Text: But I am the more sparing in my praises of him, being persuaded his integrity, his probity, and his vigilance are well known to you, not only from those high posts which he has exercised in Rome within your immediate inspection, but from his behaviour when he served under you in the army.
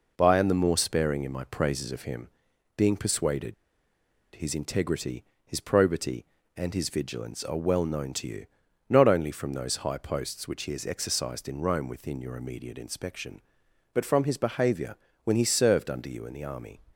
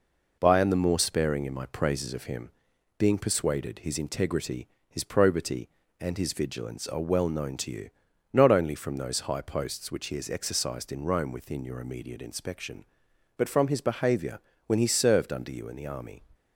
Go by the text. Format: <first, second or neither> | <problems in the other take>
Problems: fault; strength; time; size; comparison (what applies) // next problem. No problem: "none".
second | pauses between "persuaded" and "his"; noticeable; at 3.5 s; 0.80 s long // pauses between "behaviour" and "when"; slight; at 14.9 s; 0.28 s long; slight in the second